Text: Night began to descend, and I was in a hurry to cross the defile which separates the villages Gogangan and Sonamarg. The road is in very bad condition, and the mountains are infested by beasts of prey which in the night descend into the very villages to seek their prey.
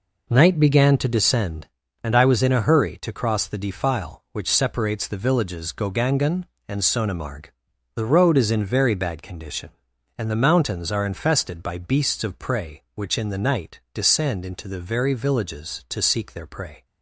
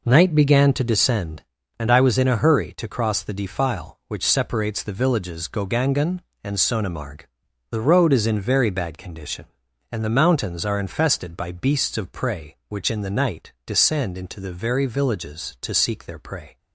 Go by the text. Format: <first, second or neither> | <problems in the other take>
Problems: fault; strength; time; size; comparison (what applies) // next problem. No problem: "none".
neither | none